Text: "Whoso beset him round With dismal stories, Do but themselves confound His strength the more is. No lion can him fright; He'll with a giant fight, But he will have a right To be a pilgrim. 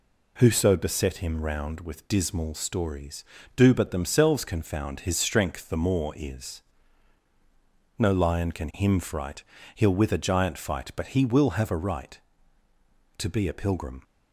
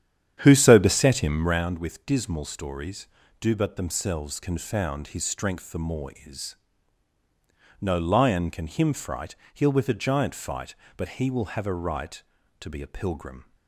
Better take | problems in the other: first | starts louder than the rest; strong; until 1.7 s; 9.5 dB

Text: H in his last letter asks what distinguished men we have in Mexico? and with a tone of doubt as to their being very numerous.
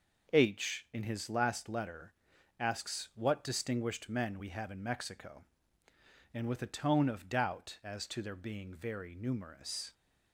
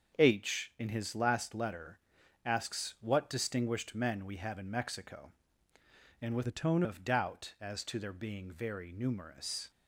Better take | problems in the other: first | starts louder than the rest; until 1.2 s; 7 dB // pauses between "letter" and "asks"; noticeable; at 1.9 s; 0.46 s long; noticeable in the first // changes voice from "a" to "tone"; from 6.4 to 6.8 s; 0.4 s long

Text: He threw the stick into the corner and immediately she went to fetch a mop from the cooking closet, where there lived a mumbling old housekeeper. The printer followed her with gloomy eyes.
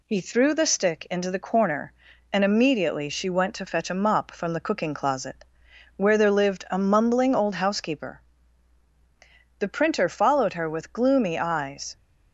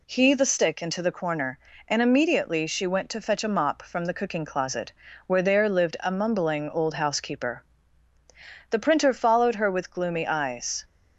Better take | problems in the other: first | skips "threw"; at 0.3 s

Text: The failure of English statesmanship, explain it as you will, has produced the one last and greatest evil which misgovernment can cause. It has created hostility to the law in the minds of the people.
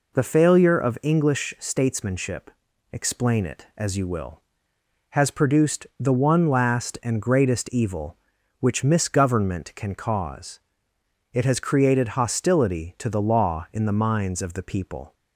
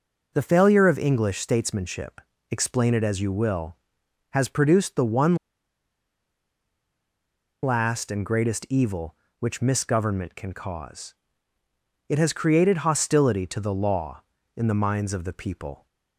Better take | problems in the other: first | pauses between "one" and "last"; strong; at 5.3 s; 2.2 s long

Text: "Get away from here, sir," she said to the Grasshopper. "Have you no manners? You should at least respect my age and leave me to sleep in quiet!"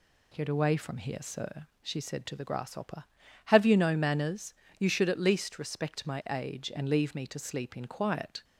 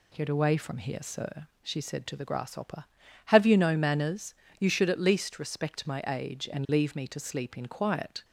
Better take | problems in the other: neither | none

